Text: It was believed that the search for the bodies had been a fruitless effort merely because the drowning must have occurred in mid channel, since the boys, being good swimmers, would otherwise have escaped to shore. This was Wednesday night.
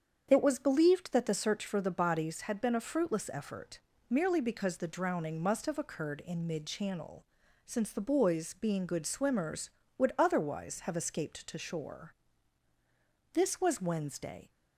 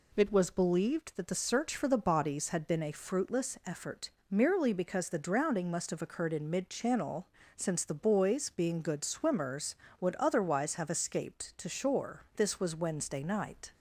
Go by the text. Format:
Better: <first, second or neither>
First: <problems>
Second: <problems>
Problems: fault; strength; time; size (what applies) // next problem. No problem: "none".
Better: second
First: starts louder than the rest; strong; until 1.3 s; 7.5 dB // pauses between "effort" and "merely"; slight; at 3.7 s; 0.32 s long // stops before "night"; at 14.4 s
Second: pauses between "effort" and "merely"; slight; at 4.0 s; 0.20 s long